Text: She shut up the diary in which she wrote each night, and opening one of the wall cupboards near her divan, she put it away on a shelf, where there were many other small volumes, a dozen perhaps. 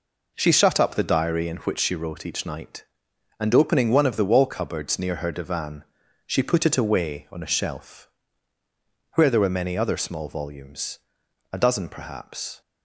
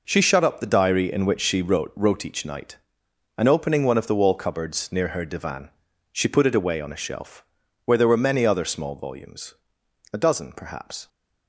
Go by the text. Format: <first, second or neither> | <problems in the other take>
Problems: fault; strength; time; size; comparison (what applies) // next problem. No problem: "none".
first | says "wrote" twice; at 1.9 s